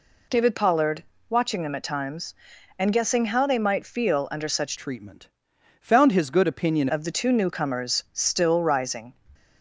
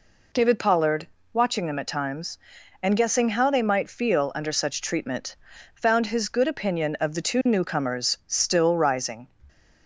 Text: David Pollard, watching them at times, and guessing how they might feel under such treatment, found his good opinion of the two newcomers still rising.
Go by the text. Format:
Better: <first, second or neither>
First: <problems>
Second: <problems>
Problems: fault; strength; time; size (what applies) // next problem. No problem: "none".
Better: second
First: changes voice from "treatment" to "opinion"; from 4.7 to 6.8 s; 2.1 s long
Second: none